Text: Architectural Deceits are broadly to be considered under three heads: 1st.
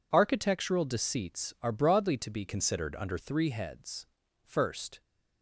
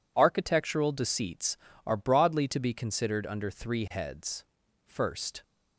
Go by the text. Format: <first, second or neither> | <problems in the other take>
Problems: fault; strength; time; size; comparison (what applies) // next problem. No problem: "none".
second | changes voice from "considered" to "under"; from 2.4 to 3.1 s; 0.7 s long